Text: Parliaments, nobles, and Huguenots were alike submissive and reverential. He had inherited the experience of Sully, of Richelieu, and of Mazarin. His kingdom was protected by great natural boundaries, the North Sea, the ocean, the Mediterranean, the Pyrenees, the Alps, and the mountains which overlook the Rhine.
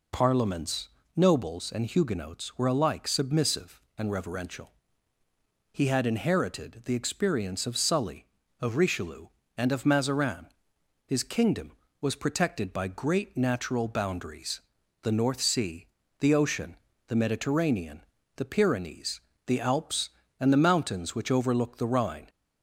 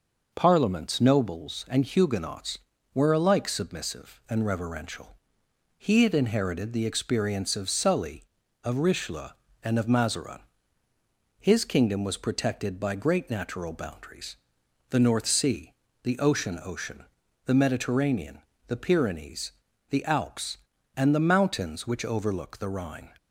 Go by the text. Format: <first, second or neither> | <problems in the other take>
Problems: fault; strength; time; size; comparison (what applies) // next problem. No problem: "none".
first | says "ocean" twice; at 16.6 s